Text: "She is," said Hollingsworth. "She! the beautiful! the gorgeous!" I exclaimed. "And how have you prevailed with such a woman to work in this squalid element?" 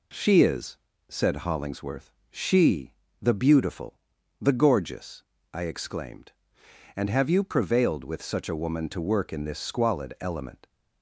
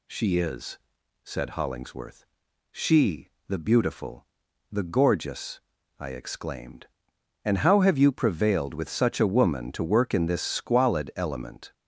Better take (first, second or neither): second